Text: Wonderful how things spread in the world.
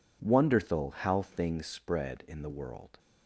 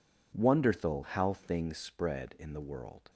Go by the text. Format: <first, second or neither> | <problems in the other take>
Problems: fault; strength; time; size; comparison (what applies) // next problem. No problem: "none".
neither | none